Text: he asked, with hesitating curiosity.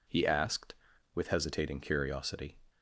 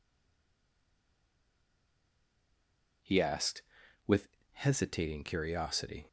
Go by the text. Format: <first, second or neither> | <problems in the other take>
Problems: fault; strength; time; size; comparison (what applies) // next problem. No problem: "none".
first | stays silent before the first word; strong; until 3.0 s; 3.0 s long // pauses between "with" and "hesitating"; slight; at 4.2 s; 0.24 s long